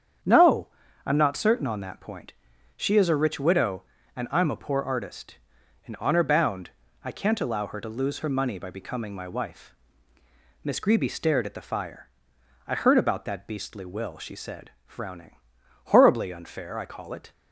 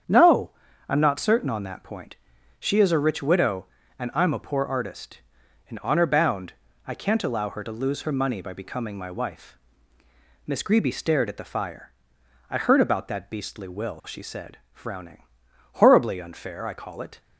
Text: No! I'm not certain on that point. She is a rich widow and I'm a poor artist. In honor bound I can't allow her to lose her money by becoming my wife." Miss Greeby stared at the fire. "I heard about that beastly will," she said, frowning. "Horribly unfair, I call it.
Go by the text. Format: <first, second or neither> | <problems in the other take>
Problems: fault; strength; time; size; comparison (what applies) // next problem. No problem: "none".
neither | starts louder than the rest; strong; the same in both // pauses between "bound" and "I"; slight; the same in both